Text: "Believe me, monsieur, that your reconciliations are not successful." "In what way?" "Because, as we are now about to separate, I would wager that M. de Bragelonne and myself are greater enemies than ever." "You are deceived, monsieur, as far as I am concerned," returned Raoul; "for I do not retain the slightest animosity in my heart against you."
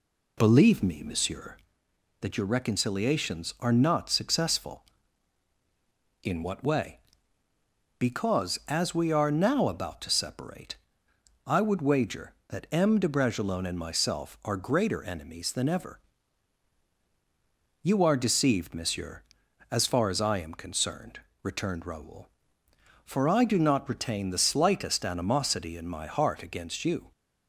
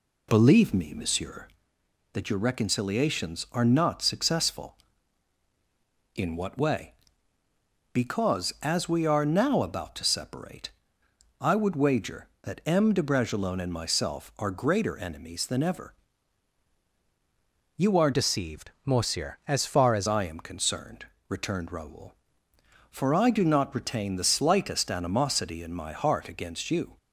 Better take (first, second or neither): first